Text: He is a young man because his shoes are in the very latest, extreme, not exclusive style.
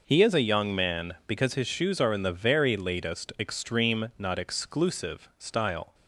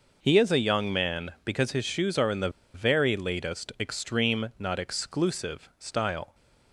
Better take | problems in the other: first | pauses between "the" and "very"; slight; at 2.5 s; 0.23 s long

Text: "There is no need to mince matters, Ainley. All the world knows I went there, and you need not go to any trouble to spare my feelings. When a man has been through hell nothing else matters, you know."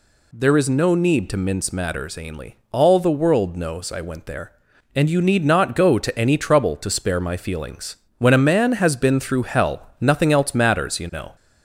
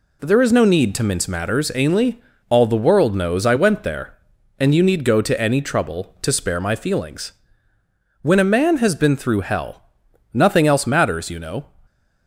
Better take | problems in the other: first | skips "not"; at 5.0 s // pauses between "hell" and "nothing"; noticeable; at 9.8 s; 0.50 s long

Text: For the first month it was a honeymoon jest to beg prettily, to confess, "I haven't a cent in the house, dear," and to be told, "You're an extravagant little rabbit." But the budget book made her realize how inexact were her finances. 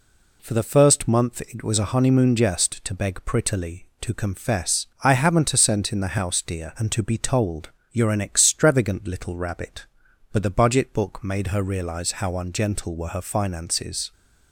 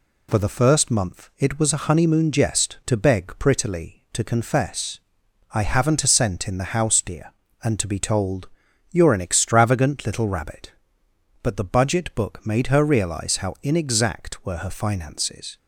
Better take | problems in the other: second | says "ungentle" for "inexact"; at 12.3 s

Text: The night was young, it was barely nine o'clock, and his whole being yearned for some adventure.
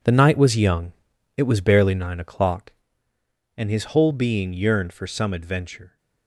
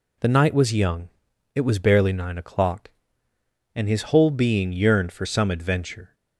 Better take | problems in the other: second | gets quieter; strong; throughout; 11.5 dB

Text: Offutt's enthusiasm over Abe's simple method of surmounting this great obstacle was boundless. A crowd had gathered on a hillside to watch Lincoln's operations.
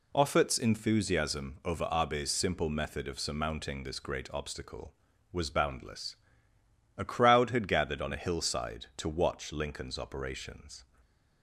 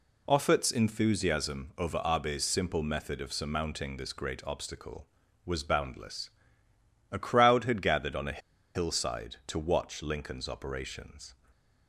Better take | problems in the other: first | pauses between "a" and "hillside"; slight; at 8.3 s; 0.36 s long // stays silent after the last word; slight; from 11.3 s on; 0.5 s long; slight in the first

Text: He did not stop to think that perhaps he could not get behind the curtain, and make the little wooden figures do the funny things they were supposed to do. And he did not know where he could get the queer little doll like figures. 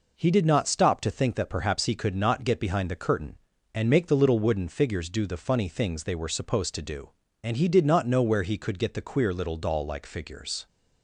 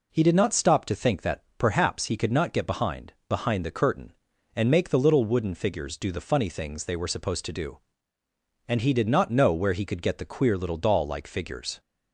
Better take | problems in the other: first | says "behind" twice; at 3.2 s

